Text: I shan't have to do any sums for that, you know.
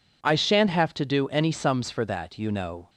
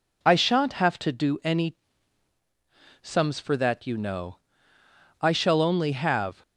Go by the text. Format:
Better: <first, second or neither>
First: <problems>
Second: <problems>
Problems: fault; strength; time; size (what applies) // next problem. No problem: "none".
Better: first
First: none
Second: pauses between "any" and "sums"; at 1.7 s; 1.2 s long // goes on to say "I shall only have"; noticeable; from 5.2 s on; 1.2 s long